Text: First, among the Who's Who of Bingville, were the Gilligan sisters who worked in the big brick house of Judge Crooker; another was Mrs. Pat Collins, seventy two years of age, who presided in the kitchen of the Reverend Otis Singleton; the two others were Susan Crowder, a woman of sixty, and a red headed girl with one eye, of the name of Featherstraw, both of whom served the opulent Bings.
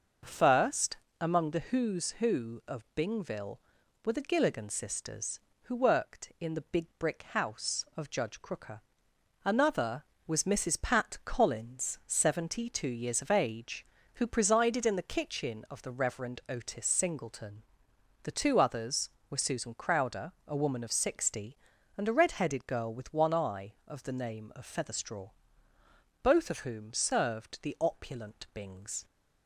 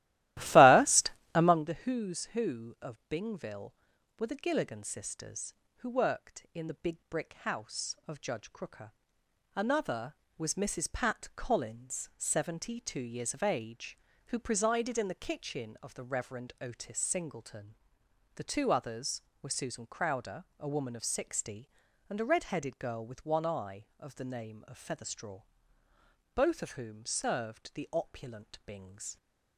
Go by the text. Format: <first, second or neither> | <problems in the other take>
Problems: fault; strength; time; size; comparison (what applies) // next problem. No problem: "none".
first | starts louder than the rest; strong; until 1.7 s; 15.5 dB